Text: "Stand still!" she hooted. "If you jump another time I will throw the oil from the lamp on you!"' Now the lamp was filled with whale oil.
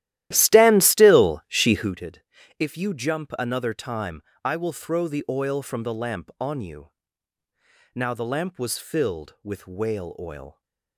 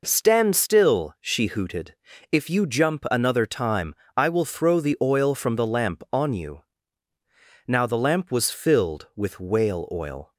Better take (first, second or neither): second